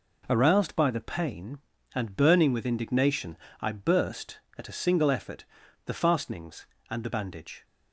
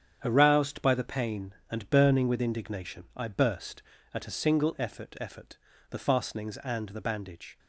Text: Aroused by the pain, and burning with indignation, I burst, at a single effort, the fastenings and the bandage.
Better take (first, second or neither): first